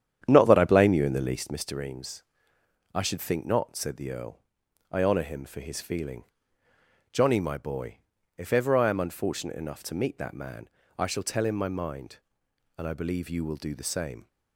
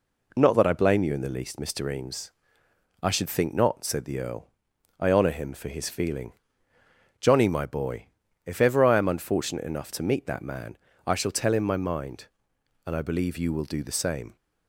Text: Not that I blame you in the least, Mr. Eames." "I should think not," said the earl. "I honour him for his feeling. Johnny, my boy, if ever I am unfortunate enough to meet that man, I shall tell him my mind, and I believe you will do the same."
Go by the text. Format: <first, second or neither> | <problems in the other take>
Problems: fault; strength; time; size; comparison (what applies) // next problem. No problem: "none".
second | starts louder than the rest; strong; until 1.6 s; 9.5 dB